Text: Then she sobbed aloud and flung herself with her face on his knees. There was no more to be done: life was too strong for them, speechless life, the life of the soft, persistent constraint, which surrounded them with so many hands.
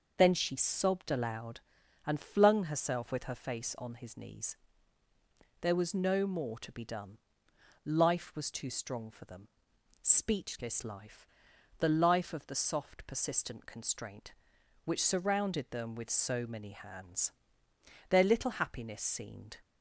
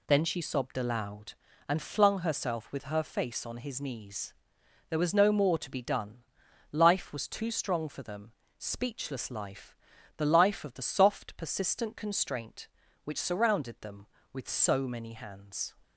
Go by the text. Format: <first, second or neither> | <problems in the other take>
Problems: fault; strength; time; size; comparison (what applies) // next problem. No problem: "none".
second | starts louder than the rest; until 1.1 s; 6 dB // goes on to say "Their little happiness seemed"; from 18.0 s on; 1.4 s long